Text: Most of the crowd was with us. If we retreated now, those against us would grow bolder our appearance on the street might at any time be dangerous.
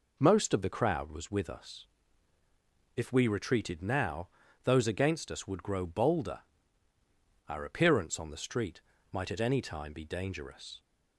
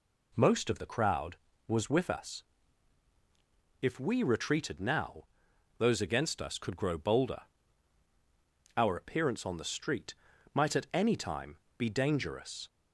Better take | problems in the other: first | says "could" for "would"; at 6.5 s // pauses between "bolder" and "our"; strong; at 7.4 s; 1.3 s long; also in the first // pauses between "street" and "might"; slight; at 10.1 s; 0.36 s long; slight in the first // pauses between "time" and "be"; slight; at 11.5 s; 0.20 s long

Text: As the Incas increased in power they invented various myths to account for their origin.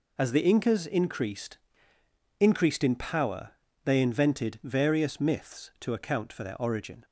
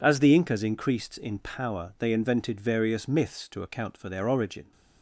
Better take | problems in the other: second | says "increased" twice; at 2.3 s // pauses between "power" and "they"; slight; at 3.5 s; 0.34 s long

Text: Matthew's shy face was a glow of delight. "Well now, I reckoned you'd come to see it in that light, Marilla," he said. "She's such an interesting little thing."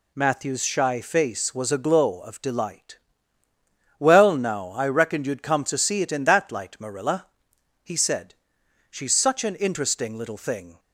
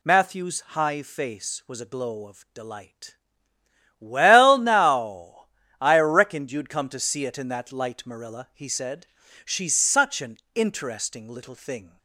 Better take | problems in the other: first | says "high" for "shy"; at 0.6 s // pauses between "an" and "interesting"; slight; at 10.3 s; 0.18 s long

